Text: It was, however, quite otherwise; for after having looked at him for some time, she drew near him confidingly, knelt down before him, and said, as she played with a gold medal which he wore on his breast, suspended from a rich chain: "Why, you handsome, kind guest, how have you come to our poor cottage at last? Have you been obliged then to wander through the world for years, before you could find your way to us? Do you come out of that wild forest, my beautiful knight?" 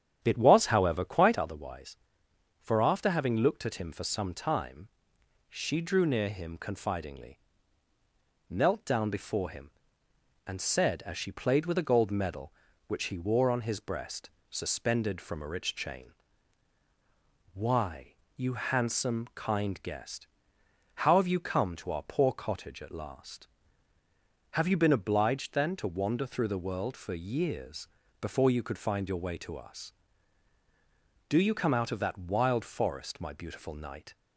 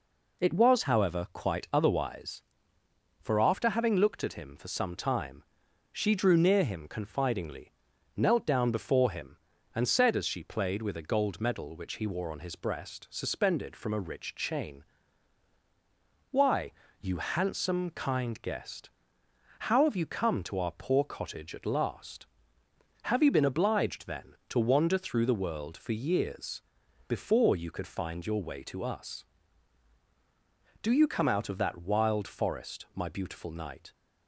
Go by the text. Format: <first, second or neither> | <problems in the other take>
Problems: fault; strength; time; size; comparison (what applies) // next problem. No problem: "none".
second | starts louder than the rest; strong; until 1.4 s; 9.5 dB